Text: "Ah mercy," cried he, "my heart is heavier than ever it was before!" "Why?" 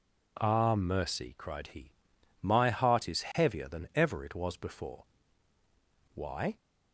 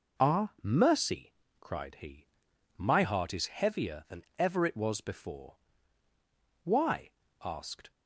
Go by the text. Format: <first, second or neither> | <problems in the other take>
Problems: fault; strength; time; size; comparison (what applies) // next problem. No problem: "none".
first | goes on to say "asked"; slight; from 7.4 s on; 0.48 s long